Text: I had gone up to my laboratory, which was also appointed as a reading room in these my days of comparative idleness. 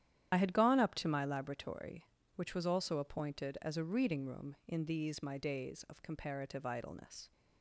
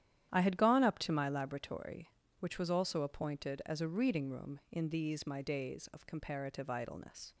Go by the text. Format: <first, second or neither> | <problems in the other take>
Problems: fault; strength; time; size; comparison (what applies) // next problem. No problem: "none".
second | loses the start of "I"; at 0.3 s; 50 ms // starts louder than the rest; strong; until 1.3 s; 10.5 dB; strong in the second